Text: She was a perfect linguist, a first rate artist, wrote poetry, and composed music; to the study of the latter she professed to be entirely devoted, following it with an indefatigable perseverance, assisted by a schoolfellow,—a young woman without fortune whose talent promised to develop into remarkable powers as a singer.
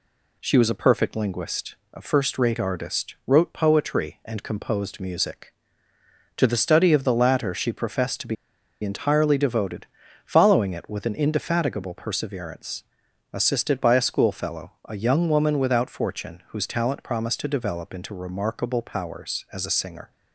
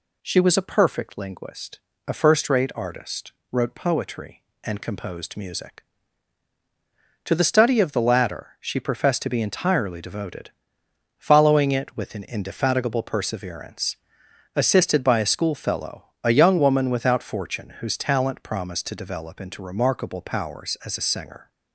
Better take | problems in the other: second | pauses between "be" and "entirely"; noticeable; at 8.3 s; 0.47 s long

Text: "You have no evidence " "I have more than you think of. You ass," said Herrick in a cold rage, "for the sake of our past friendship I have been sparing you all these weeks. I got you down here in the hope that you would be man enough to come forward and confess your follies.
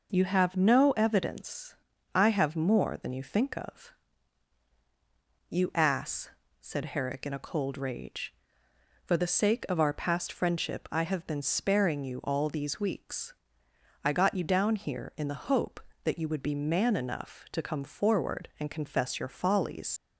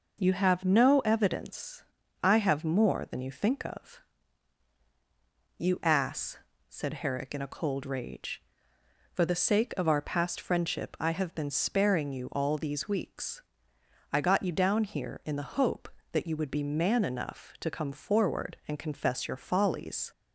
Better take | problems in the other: second | leaves "follies" unfinished; at 19.9 s; 65 ms

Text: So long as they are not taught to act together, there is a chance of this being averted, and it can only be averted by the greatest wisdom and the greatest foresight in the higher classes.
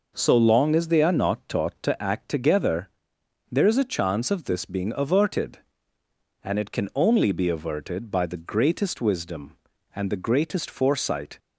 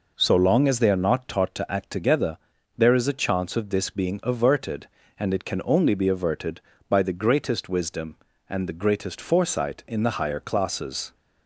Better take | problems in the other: second | stops before "in the higher classes"; at 11.3 s

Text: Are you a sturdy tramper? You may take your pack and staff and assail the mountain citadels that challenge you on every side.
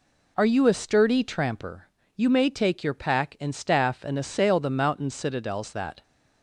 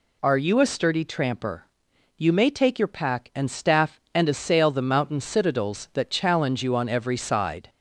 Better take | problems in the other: second | stops before "challenge you on every side"; at 6.0 s

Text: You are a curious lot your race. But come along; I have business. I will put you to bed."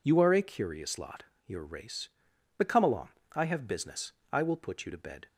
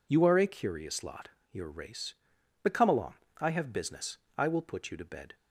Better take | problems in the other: neither | pauses between "lot" and "your"; slight; the same in both

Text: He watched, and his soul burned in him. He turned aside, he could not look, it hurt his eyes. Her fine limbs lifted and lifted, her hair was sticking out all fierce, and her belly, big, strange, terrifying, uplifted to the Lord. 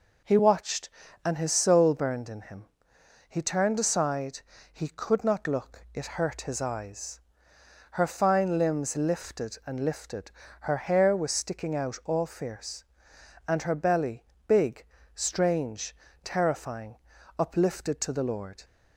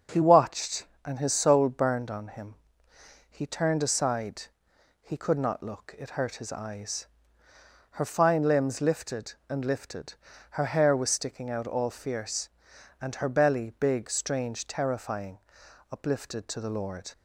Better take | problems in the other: first | starts louder than the rest; until 1.3 s; 6.5 dB // says "on" for "in"; at 2.1 s

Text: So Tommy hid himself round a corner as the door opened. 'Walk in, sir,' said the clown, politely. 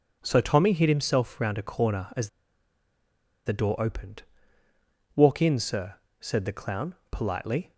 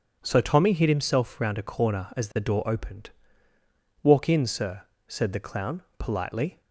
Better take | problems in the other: second | pauses between "as" and "the"; at 2.2 s; 1.1 s long

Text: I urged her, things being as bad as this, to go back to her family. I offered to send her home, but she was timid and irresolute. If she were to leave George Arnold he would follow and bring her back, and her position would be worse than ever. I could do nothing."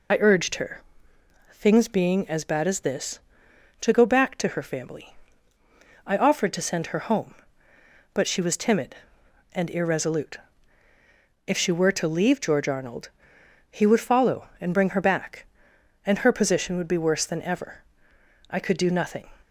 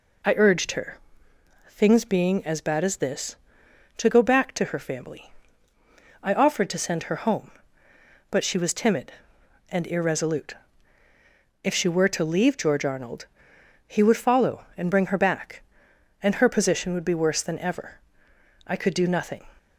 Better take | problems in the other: second | loses the start of "I"; at 0.1 s; 25 ms // pauses between "Arnold" and "he"; noticeable; at 13.0 s; 0.62 s long; noticeable in the second

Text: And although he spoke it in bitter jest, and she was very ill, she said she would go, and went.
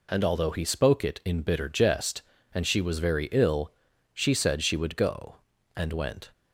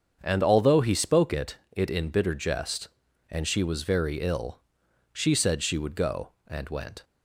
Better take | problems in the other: first | starts louder than the rest; strong; until 1.2 s; 7 dB // says "it" twice; at 1.7 s

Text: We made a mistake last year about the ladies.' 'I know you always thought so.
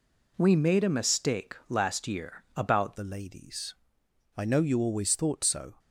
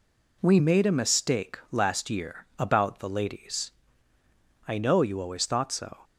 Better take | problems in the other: second | changes voice at "the"; from 2.9 s on; 2.8 s long

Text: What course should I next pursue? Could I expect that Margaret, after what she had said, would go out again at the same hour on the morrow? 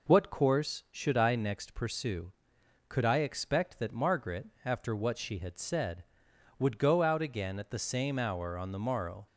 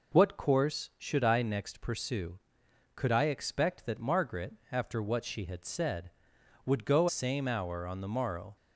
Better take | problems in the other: first | skips "out again at the"; at 7.0 s

